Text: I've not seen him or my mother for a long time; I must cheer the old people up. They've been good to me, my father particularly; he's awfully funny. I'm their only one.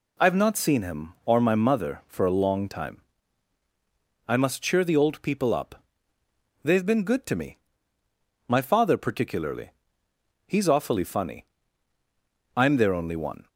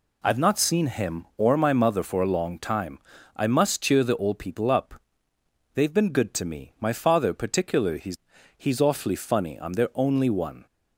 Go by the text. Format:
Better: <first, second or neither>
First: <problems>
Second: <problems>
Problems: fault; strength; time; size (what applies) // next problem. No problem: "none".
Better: first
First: none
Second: says "he's" twice; at 8.5 s